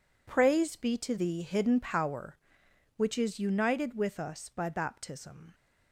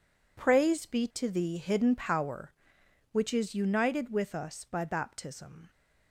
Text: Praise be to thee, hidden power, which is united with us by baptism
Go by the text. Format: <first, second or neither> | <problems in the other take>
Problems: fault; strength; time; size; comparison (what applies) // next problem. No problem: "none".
neither | none